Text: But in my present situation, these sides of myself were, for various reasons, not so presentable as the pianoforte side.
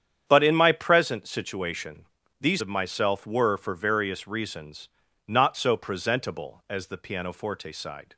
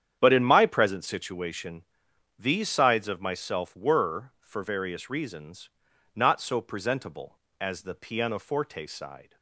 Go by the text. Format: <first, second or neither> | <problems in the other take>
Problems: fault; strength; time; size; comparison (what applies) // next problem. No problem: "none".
second | starts louder than the rest; strong; until 1.2 s; 8.5 dB; strong in the second // skips "sides"; at 2.6 s